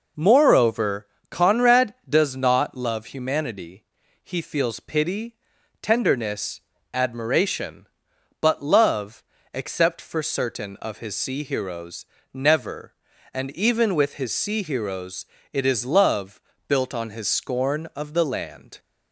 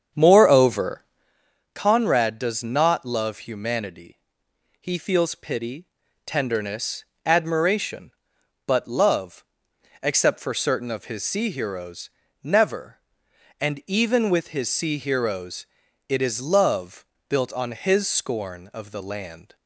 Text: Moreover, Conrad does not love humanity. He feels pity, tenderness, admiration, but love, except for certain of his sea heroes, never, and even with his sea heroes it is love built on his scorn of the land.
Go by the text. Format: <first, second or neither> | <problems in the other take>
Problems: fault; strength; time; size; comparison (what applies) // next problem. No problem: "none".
first | starts louder than the rest; strong; until 1.3 s; 7.5 dB // pauses between "heroes" and "it"; at 15.6 s; 0.44 s long; slight in the first // pauses between "love" and "built"; slight; at 17.0 s; 0.24 s long; slight in the first